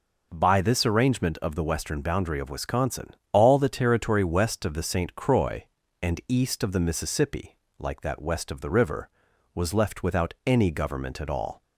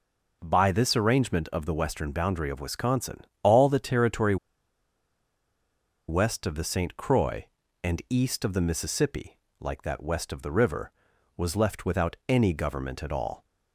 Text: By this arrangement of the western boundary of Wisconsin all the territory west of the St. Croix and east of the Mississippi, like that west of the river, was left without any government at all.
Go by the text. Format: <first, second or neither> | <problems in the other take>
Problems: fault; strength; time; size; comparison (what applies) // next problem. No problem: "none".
first | pauses between "Wisconsin" and "all"; slight; at 3.2 s; 0.20 s long; slight in the first // pauses between "territory" and "west"; strong; at 4.3 s; 1.7 s long